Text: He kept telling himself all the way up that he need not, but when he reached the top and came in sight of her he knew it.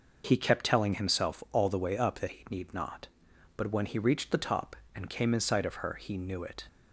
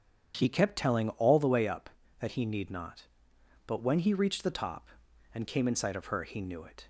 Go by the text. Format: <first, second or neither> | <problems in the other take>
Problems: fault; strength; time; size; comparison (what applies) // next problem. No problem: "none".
first | starts louder than the rest; strong; until 1.4 s; 8.5 dB // skips "himself"; at 1.0 s